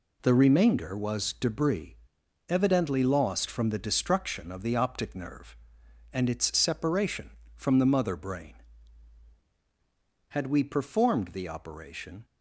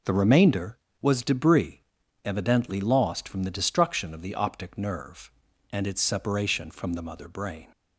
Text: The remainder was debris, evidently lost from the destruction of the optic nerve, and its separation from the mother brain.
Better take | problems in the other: second | goes on to say "Had we performed the operation"; strong; from 10.2 s on; 1.9 s long

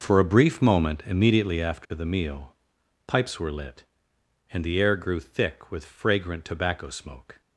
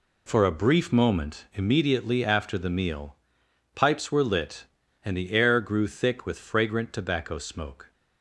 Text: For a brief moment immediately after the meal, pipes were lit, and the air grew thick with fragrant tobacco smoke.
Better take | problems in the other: neither | none

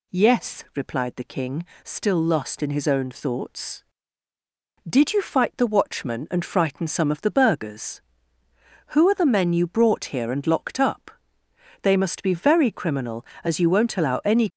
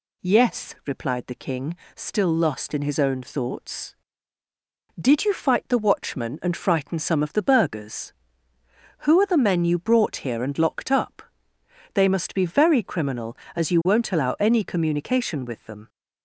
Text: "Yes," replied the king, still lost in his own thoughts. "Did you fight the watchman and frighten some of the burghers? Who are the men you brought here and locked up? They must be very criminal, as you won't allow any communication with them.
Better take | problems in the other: second | stops before "communication with them"; at 14.4 s

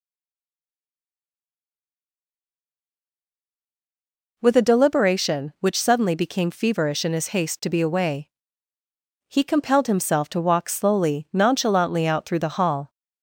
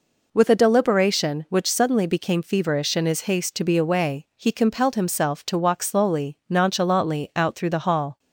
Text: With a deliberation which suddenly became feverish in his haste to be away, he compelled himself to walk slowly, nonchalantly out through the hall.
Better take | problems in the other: second | stays silent before the first word; strong; until 4.3 s; 4.3 s long

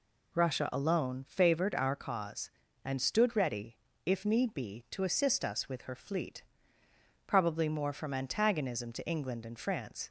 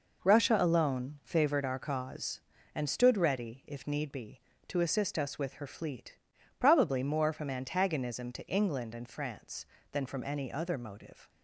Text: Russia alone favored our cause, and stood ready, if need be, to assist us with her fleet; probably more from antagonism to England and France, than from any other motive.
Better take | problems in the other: second | stops before "than from any other motive"; at 10.0 s

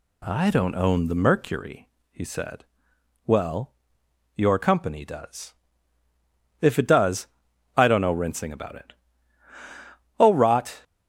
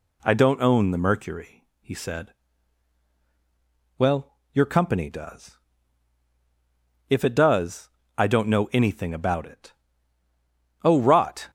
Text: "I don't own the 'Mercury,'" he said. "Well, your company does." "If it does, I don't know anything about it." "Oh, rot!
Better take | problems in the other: second | says "rinsing" for "anything"; at 8.1 s

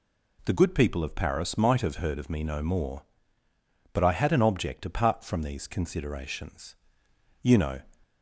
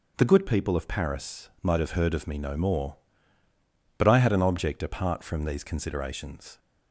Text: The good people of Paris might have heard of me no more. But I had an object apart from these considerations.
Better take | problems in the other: second | goes on to say "You know"; slight; from 7.4 s on; 0.38 s long

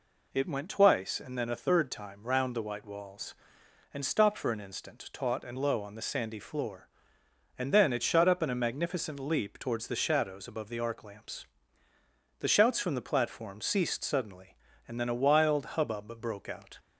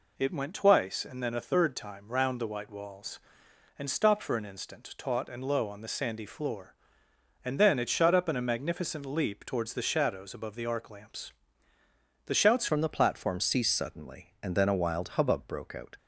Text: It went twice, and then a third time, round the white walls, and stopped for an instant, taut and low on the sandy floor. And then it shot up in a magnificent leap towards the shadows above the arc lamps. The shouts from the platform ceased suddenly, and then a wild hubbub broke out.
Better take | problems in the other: first | changes voice at "from"; from 12.6 s on; 3.3 s long

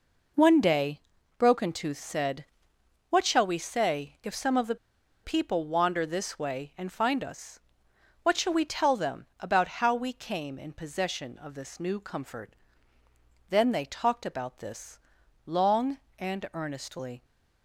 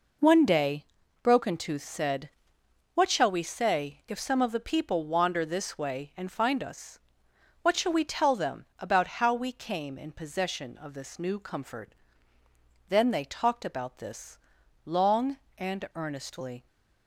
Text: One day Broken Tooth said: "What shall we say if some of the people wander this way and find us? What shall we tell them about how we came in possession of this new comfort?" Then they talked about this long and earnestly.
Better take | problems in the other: second | pauses between "day" and "Broken"; at 0.9 s; 0.38 s long; also in the second // pauses between "the" and "people"; noticeable; at 4.7 s; 0.48 s long // pauses between "this" and "long"; noticeable; at 14.9 s; 0.46 s long; noticeable in the second

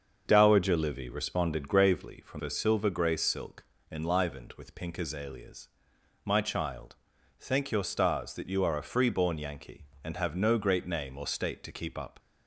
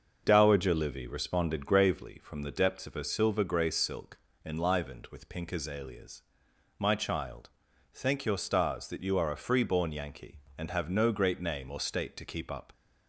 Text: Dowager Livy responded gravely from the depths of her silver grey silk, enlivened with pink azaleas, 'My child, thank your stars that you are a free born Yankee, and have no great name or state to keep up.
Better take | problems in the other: second | starts louder than the rest; until 1.2 s; 6.5 dB; also in the second // skips "the depths of"; at 2.4 s

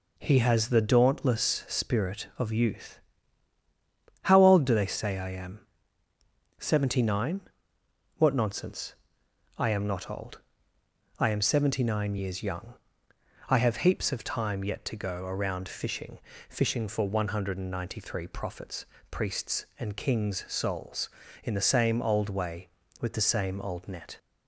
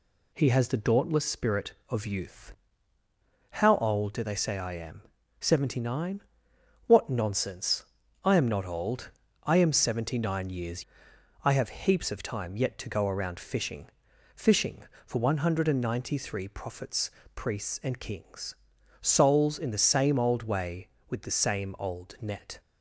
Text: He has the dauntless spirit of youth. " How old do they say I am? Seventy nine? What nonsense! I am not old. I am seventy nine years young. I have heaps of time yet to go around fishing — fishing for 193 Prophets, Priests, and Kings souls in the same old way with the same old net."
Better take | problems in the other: first | skips "young"; at 11.1 s // pauses between "Kings" and "souls"; noticeable; at 18.5 s; 0.48 s long

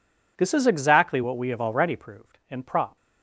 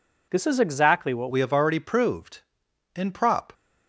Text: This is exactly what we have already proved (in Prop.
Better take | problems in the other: first | changes voice at "we"; from 1.2 s on; 2.3 s long

